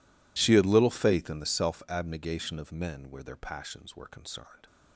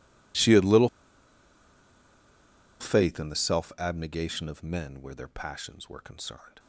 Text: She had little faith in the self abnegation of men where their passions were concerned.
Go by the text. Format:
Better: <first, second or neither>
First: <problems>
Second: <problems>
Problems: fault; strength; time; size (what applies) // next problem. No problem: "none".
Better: first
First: none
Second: pauses between "little" and "faith"; strong; at 0.8 s; 1.9 s long